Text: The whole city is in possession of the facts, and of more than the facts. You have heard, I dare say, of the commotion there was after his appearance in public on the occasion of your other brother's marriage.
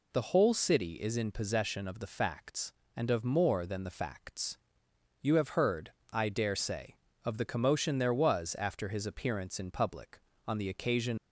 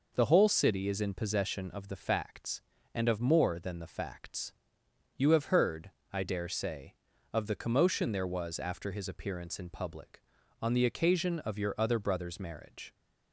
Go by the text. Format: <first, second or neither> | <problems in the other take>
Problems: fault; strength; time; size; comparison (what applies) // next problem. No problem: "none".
second | stops before "of your other brother's marriage"; at 11.1 s